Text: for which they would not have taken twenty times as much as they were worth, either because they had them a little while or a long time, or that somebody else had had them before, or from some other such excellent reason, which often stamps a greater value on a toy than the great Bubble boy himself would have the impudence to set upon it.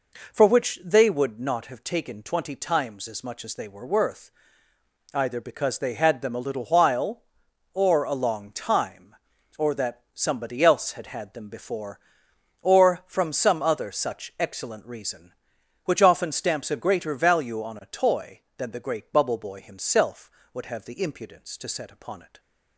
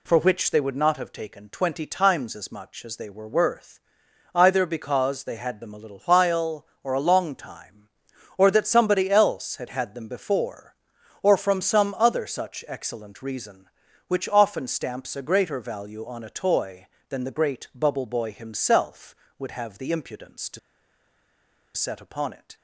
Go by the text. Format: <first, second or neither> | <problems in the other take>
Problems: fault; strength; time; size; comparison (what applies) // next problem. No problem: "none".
first | pauses between "to" and "set"; at 20.5 s; 1.1 s long